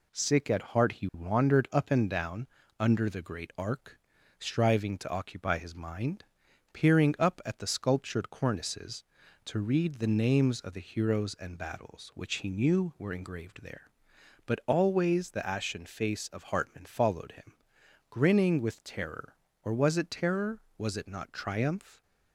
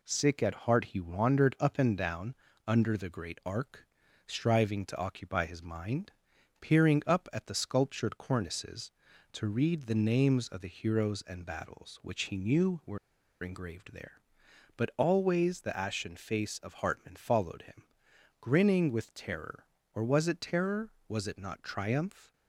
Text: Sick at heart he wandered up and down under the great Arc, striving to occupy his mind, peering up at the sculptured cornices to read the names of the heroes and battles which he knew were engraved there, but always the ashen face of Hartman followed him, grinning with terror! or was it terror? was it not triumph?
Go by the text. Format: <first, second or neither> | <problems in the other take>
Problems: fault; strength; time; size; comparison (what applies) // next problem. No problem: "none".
first | pauses between "down" and "under"; slight; at 2.3 s; 0.32 s long; slight in the first // pauses between "were" and "engraved"; at 12.9 s; 0.44 s long